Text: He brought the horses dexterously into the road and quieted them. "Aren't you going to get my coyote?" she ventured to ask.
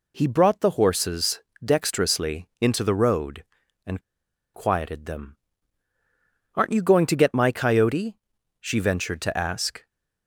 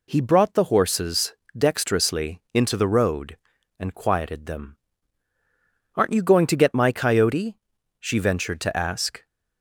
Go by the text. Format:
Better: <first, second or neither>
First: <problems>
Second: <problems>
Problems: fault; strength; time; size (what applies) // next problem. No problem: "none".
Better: second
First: pauses between "horses" and "dexterously"; slight; at 1.4 s; 0.20 s long // pauses between "and" and "quieted"; noticeable; at 3.9 s; 0.54 s long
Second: pauses between "horses" and "dexterously"; slight; at 1.3 s; 0.20 s long